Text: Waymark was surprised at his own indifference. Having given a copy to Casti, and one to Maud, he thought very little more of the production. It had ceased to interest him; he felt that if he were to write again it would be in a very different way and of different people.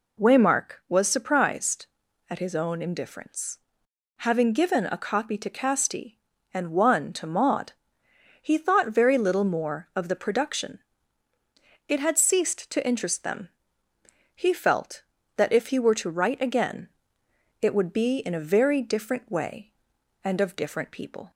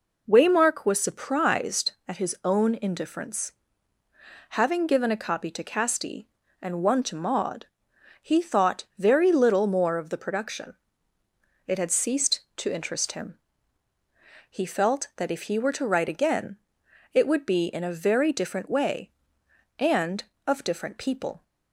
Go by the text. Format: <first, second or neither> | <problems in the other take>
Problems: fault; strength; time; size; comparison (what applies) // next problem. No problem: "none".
second | says "them" for "him"; at 13.2 s // pauses between "again" and "it"; noticeable; at 16.8 s; 0.74 s long; noticeable in the second